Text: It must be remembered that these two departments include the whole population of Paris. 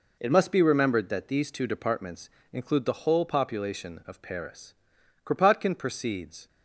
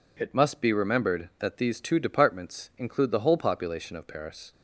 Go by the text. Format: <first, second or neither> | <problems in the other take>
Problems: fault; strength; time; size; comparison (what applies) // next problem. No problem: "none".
second | pauses between "departments" and "include"; slight; at 2.2 s; 0.24 s long // goes on to say "Kropotkin proceeds"; noticeable; from 5.2 s on; 1.2 s long